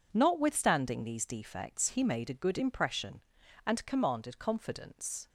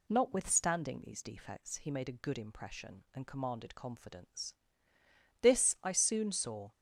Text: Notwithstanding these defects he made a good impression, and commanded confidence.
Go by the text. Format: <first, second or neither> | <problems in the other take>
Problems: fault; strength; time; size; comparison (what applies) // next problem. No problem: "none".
first | goes on to say "This I soon saw"; from 5.3 s on; 1.3 s long